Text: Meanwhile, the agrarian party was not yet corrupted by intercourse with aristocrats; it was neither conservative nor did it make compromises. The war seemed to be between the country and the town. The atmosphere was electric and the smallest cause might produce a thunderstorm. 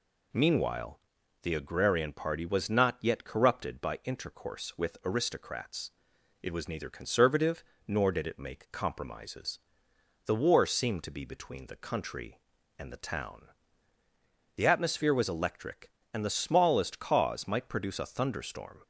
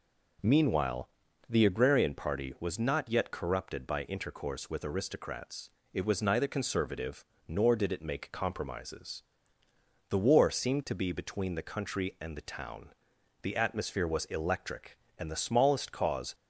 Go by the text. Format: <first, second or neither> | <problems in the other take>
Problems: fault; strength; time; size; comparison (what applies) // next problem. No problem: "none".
first | pauses between "conservative" and "nor"; slight; at 7.2 s; 0.20 s long; slight in the first // stops before "might produce a thunderstorm"; at 16.3 s